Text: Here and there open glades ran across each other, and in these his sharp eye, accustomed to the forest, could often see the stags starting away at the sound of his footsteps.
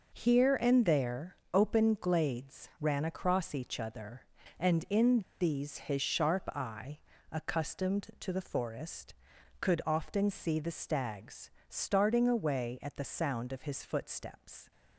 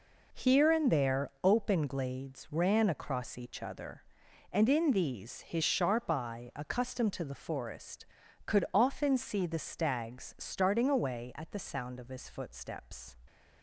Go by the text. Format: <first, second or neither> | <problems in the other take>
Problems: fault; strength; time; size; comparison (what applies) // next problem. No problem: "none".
second | pauses between "in" and "these"; slight; at 5.2 s; 0.19 s long // pauses between "stags" and "starting"; slight; at 11.5 s; 0.18 s long